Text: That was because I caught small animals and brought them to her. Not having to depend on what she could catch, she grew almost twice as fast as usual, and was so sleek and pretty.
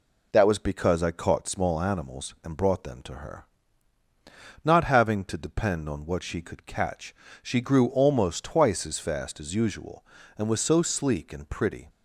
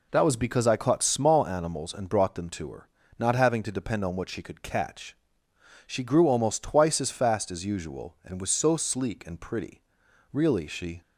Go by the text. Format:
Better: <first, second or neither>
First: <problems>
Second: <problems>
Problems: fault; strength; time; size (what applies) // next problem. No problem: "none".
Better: first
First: none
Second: goes on to say "Really she"; noticeable; from 10.3 s on; 0.70 s long